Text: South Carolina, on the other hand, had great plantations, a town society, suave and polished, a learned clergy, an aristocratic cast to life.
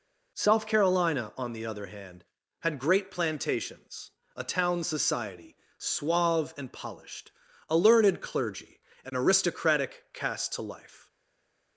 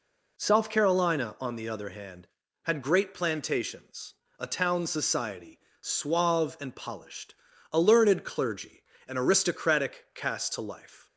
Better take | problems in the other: second | stays silent after the last word; slight; from 11.0 s on; 0.7 s long

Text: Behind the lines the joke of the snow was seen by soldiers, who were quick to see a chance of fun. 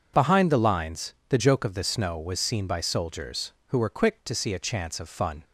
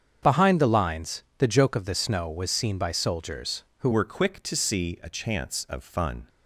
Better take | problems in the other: first | starts louder than the rest; strong; until 1.4 s; 7.5 dB // pauses between "lines" and "the"; slight; at 1.2 s; 0.16 s long; slight in the first // changes voice at "were"; from 3.9 s on; 2.3 s long

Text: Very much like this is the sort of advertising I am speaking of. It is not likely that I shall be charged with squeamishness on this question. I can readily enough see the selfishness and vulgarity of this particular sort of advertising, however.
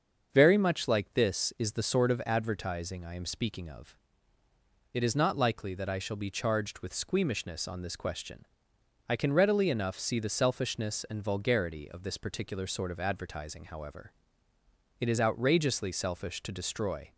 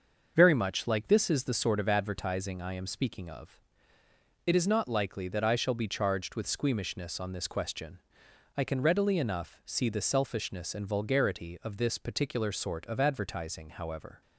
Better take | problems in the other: second | starts louder than the rest; until 1.3 s; 6.5 dB; also in the second // goes on to say "It is outrageously selfish to destroy"; strong; from 14.9 s on; 2.1 s long

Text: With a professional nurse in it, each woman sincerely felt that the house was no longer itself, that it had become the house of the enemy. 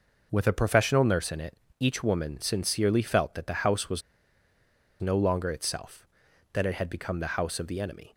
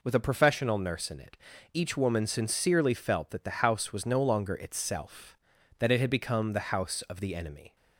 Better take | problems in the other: second | pauses between "was" and "no"; at 4.0 s; 1.0 s long

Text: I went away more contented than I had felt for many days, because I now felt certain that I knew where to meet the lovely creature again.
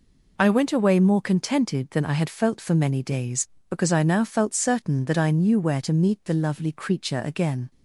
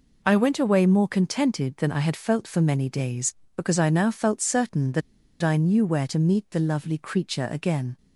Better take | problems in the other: first | pauses between "that" and "I"; at 5.0 s; 0.41 s long

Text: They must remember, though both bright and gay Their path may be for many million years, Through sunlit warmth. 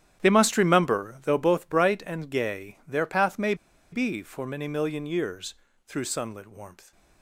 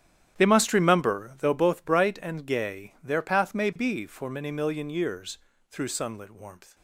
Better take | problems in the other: second | starts louder than the rest; strong; until 1.2 s; 10.5 dB; strong in the second // pauses between "may" and "be"; at 3.5 s; 0.37 s long

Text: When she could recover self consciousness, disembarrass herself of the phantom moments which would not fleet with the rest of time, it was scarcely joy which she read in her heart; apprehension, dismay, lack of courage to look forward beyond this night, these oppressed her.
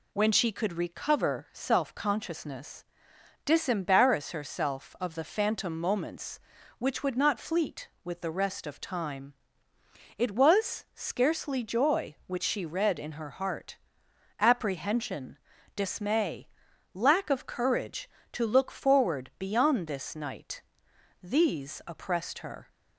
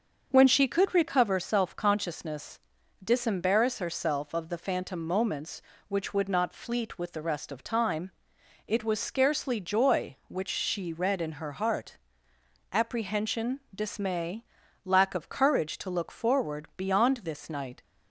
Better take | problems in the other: first | starts louder than the rest; until 1.3 s; 6.5 dB // stops before "these oppressed her"; at 17.8 s

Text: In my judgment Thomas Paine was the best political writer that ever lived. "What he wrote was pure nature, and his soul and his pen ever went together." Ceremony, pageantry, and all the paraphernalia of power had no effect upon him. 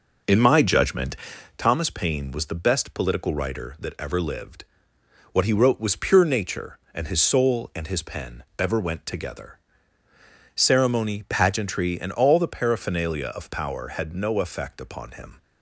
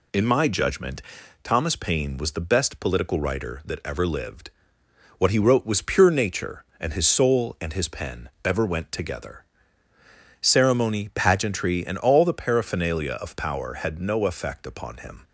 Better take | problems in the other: second | starts louder than the rest; noticeable; until 1.8 s; 5 dB // pauses between "judgment" and "Thomas"; at 1.1 s; 0.42 s long; also in the second // pauses between "pen" and "ever"; slight; at 8.4 s; 0.16 s long; slight in the second

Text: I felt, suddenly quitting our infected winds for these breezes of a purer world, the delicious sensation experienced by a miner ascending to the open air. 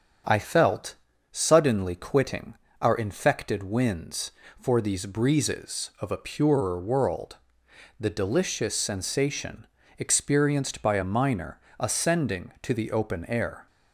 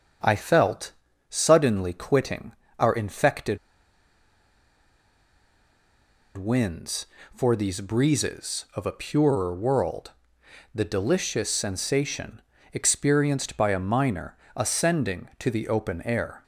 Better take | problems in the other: first | starts louder than the rest; strong; until 1.6 s; 7.5 dB; strong in the first // pauses between "quitting" and "our"; slight; at 2.5 s; 0.26 s long; slight in the first // pauses between "infected" and "winds"; strong; at 3.5 s; 2.7 s long // pauses between "sensation" and "experienced"; slight; at 12.4 s; 0.32 s long; slight in the first // pauses between "miner" and "ascending"; slight; at 14.3 s; 0.22 s long; slight in the first

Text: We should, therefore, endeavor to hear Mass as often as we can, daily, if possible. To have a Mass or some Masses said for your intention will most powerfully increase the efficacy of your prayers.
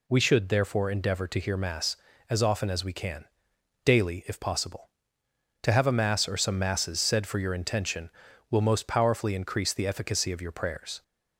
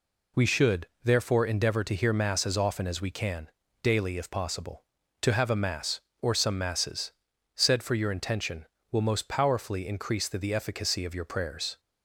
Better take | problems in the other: first | pauses between "Masses" and "said"; at 7.1 s; 0.44 s long // says "the" twice; at 10.3 s

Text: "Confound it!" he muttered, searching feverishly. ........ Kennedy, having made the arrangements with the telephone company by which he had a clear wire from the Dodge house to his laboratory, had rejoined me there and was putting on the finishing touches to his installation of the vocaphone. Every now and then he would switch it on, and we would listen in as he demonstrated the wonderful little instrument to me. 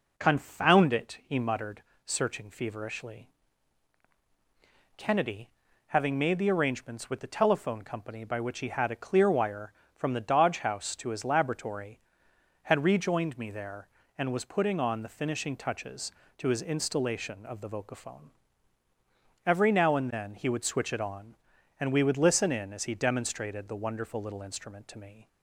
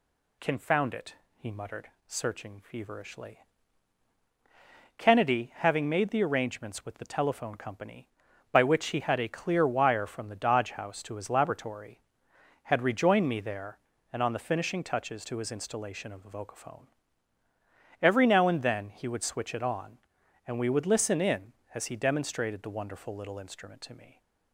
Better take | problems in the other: first | skips "was putting"; at 14.2 s

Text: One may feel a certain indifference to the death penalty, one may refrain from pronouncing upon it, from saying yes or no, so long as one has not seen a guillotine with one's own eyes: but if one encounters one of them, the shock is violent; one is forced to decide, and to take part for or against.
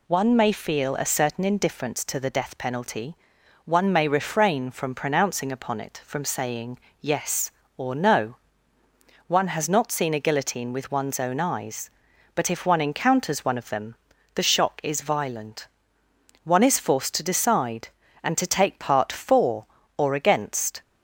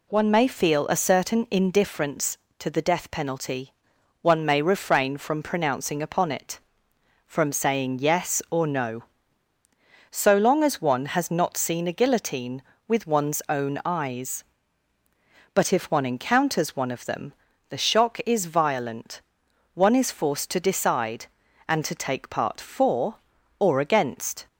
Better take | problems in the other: second | pauses between "saying" and "yes"; slight; at 6.7 s; 0.22 s long // skips "so long as"; at 8.8 s

